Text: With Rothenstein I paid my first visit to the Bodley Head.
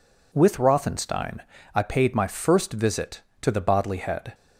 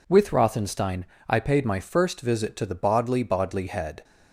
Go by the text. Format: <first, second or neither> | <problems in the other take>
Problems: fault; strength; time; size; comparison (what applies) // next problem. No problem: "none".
first | pauses between "Rothenstein" and "I"; slight; at 1.0 s; 0.24 s long; slight in the first // says "Bodley" twice; at 3.2 s